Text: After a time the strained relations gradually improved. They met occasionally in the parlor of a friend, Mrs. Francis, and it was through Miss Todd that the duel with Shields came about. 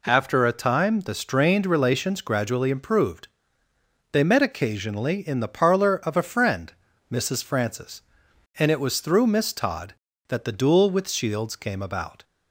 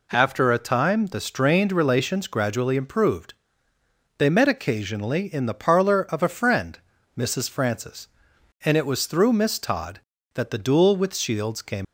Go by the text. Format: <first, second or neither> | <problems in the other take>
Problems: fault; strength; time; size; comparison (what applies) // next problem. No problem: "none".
first | stops before "about"; at 11.8 s